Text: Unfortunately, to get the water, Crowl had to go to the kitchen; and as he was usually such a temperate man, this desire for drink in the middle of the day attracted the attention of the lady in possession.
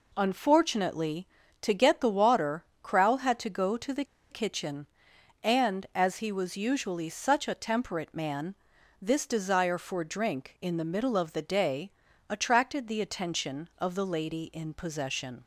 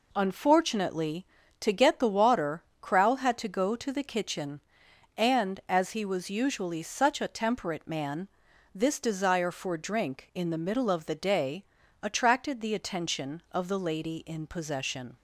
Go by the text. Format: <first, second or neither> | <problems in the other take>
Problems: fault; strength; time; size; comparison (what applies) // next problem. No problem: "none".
second | pauses between "the" and "kitchen"; slight; at 4.0 s; 0.26 s long // pauses between "day" and "attracted"; at 11.8 s; 0.40 s long; also in the second